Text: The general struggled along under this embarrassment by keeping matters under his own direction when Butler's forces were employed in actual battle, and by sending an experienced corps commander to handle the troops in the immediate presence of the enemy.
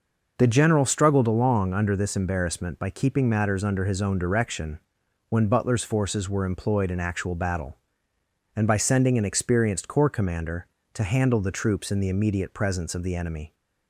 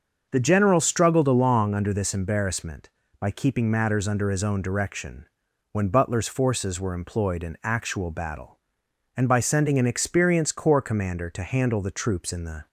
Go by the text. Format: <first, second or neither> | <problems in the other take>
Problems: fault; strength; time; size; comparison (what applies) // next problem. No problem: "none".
first | starts louder than the rest; until 1.3 s; 6.5 dB // pauses between "direction" and "when"; noticeable; at 5.2 s; 0.46 s long; noticeable in the first // stops before "immediate presence of the enemy"; at 12.6 s